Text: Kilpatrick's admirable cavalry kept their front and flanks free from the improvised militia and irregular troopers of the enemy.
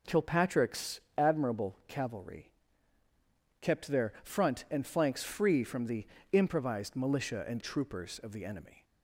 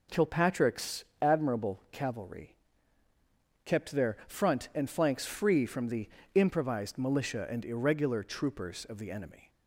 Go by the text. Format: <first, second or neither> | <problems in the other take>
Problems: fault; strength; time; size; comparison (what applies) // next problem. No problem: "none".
second | pauses between "Kilpatrick's" and "admirable"; slight; at 0.9 s; 0.18 s long; slight in the second // pauses between "cavalry" and "kept"; at 2.5 s; 1.0 s long; also in the second // pauses between "the" and "improvised"; slight; at 6.0 s; 0.26 s long; slight in the second // skips "irregular"; at 7.6 s